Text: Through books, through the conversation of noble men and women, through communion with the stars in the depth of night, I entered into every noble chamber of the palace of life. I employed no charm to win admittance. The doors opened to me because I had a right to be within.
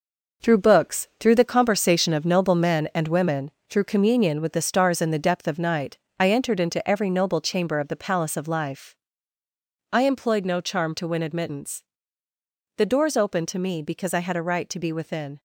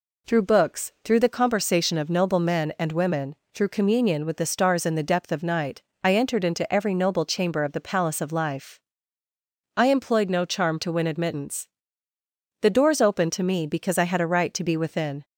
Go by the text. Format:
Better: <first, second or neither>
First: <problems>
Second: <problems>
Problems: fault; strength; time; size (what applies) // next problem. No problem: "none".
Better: second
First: gets quieter; strong; throughout; 8 dB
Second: none